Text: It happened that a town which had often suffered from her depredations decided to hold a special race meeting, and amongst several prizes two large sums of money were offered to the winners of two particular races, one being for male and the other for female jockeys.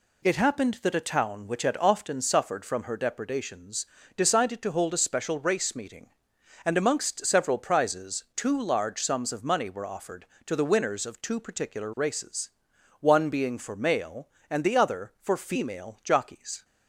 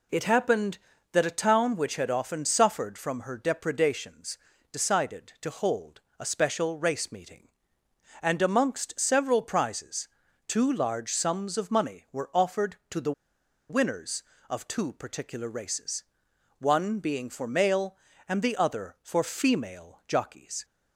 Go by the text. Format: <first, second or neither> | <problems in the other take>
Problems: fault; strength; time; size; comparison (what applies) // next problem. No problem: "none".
first | pauses between "depredations" and "decided"; slight; at 4.3 s; 0.34 s long; slight in the first // pauses between "hold" and "a"; slight; at 6.0 s; 0.18 s long // pauses between "prizes" and "two"; at 10.0 s; 0.40 s long // pauses between "the" and "winners"; noticeable; at 13.1 s; 0.58 s long